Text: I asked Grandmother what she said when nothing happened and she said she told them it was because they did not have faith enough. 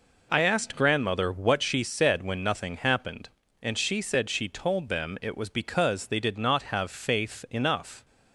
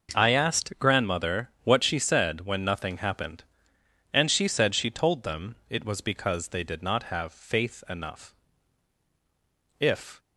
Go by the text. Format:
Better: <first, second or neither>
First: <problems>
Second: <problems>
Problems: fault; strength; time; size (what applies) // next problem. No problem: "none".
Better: first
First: none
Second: pauses between "them" and "it"; slight; at 5.5 s; 0.16 s long // goes on to say "If"; slight; from 9.7 s on; 0.40 s long